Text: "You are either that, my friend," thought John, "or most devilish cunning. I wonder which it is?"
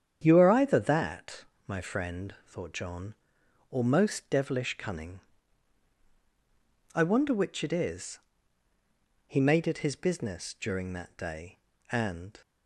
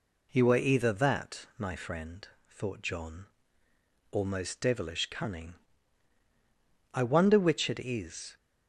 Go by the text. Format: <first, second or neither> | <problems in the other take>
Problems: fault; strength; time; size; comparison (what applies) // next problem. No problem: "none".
second | starts louder than the rest; strong; until 1.2 s; 8.5 dB // goes on to say "He made it his business during that day and"; strong; from 9.2 s on; 3.1 s long